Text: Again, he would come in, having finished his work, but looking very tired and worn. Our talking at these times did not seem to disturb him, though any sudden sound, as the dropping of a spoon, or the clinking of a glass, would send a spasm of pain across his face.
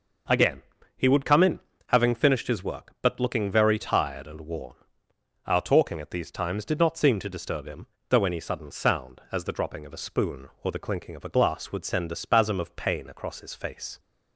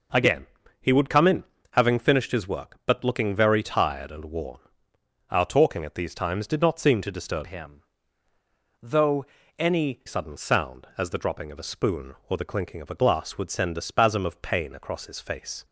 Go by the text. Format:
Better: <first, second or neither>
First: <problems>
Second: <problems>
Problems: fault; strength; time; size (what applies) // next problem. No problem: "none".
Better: first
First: none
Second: changes voice from "him" to "any"; from 7.4 to 10.0 s; 2.6 s long // pauses between "though" and "any"; slight; at 9.2 s; 0.34 s long